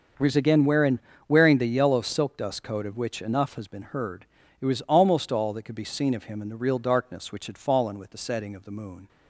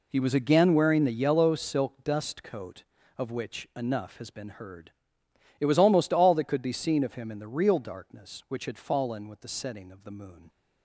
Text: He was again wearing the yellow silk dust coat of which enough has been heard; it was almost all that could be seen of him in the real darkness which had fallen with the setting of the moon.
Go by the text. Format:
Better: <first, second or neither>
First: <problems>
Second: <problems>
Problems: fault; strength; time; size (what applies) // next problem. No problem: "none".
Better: second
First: starts louder than the rest; until 1.4 s; 6 dB // says "wearing" twice; at 1.2 s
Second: none